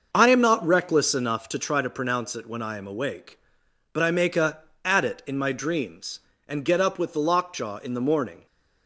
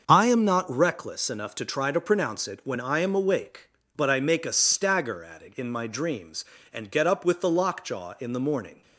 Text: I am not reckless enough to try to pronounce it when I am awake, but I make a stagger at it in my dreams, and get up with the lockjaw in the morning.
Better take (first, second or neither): second